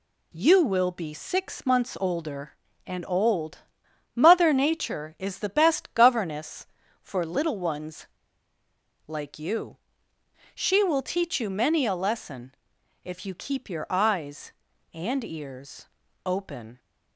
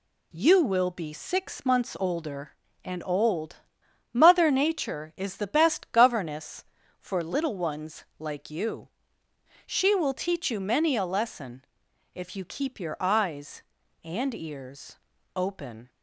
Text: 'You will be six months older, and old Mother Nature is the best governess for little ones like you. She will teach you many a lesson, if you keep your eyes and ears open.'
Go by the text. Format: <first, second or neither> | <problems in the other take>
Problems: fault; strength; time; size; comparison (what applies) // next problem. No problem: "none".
second | pauses between "old" and "Mother"; noticeable; at 3.5 s; 0.56 s long; noticeable in the second // pauses between "ones" and "like"; at 8.0 s; 0.98 s long // pauses between "ears" and "open"; at 15.8 s; 0.38 s long; also in the second